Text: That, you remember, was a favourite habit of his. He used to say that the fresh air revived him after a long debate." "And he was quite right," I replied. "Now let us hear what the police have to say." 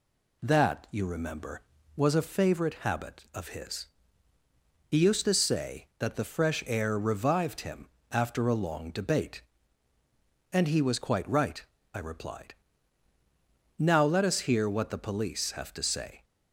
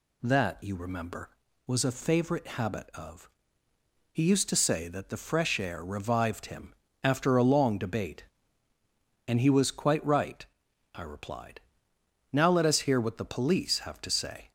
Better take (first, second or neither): first